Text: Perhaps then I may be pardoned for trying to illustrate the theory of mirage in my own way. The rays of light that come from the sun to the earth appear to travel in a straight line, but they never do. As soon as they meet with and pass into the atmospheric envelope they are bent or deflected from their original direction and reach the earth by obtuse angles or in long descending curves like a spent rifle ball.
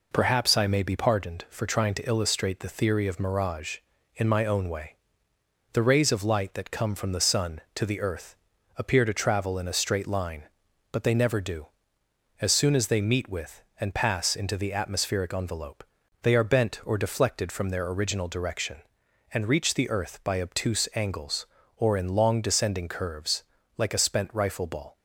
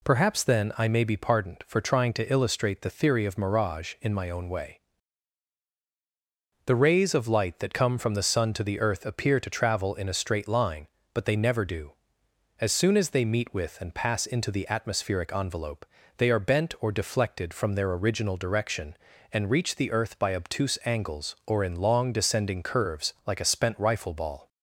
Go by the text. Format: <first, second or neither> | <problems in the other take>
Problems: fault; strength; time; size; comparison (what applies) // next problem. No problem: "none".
second | skips "then"; at 0.5 s // pauses between "earth" and "appear"; at 8.3 s; 0.42 s long // pauses between "envelope" and "they"; at 15.8 s; 0.38 s long; slight in the second // pauses between "curves" and "like"; slight; at 23.4 s; 0.34 s long